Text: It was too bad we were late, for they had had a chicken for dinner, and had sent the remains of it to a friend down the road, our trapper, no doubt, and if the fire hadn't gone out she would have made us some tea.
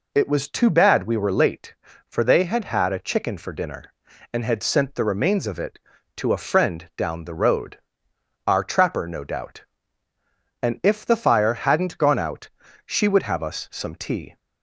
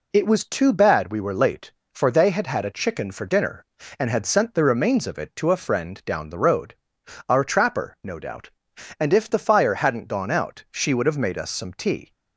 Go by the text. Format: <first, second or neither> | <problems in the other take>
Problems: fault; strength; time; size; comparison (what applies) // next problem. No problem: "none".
second | pauses between "out" and "she"; at 12.4 s; 0.38 s long // skips "made"; at 13.4 s